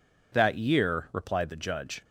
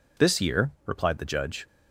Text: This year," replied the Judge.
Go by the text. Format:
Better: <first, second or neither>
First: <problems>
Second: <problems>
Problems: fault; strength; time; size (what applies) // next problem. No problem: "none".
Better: second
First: says "That" for "This"; at 0.3 s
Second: none